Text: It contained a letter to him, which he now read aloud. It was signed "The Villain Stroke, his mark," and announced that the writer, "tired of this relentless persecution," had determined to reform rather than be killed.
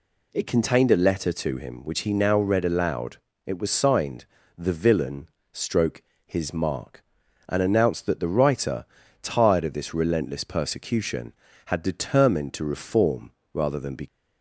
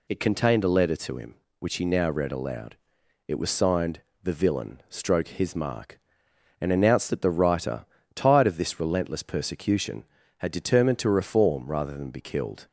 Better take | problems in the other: second | pauses between "signed" and "The"; slight; at 4.2 s; 0.32 s long; slight in the second // pauses between "Villain" and "Stroke"; slight; at 5.2 s; 0.24 s long // pauses between "reform" and "rather"; slight; at 13.3 s; 0.20 s long // stops before "killed"; at 14.0 s

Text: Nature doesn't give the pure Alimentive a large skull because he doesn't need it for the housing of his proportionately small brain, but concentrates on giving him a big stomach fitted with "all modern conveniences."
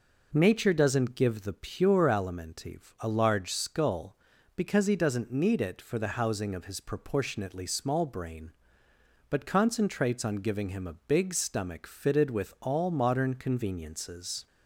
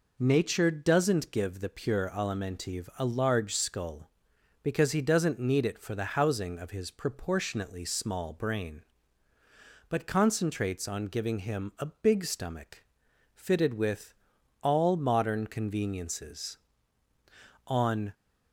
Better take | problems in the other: first | pauses between "stomach" and "fitted"; noticeable; at 12.8 s; 0.50 s long // pauses between "with" and "all"; noticeable; at 14.1 s; 0.48 s long // goes on to say "On"; slight; from 17.6 s on; 0.48 s long

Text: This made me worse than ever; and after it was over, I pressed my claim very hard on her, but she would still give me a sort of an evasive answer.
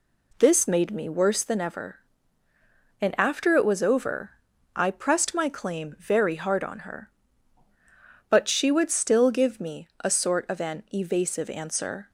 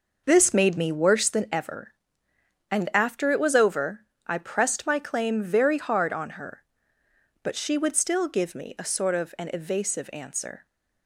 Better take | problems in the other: first | starts louder than the rest; noticeable; until 1.6 s; 5.5 dB

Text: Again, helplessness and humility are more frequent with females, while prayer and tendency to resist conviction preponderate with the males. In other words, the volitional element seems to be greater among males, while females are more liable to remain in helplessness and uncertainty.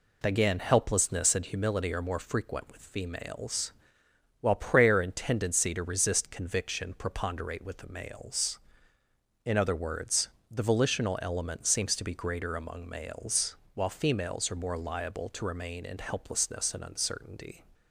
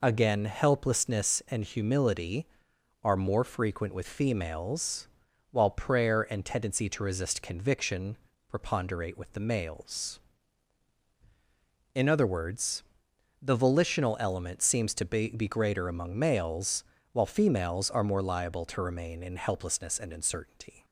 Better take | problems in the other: first | pauses between "conviction" and "preponderate"; slight; at 8.1 s; 0.32 s long // says "be" twice; at 15.2 s

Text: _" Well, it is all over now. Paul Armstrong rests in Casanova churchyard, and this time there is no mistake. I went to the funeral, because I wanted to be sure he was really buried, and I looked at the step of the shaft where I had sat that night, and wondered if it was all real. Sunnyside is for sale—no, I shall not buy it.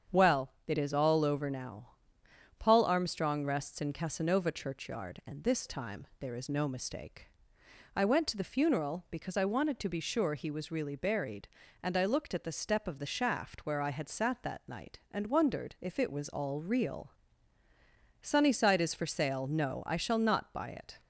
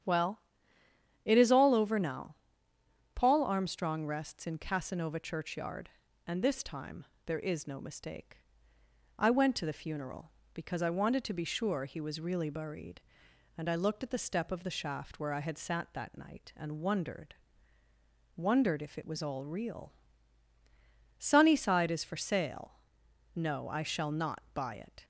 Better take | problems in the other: first | starts louder than the rest; strong; until 1.8 s; 9 dB; strong in the first // pauses between "time" and "there"; slight; at 7.0 s; 0.20 s long // says "wondered" twice; at 18.3 s

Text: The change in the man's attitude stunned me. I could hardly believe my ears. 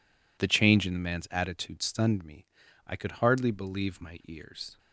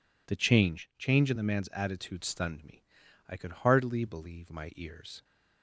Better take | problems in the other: first | says "change" twice; at 0.9 s

